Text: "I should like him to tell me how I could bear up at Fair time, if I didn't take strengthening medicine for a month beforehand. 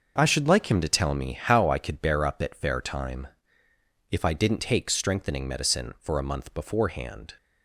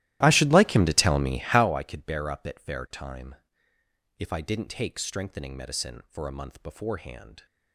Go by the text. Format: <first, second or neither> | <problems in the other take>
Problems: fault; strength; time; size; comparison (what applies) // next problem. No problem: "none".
first | starts louder than the rest; strong; until 1.8 s; 15 dB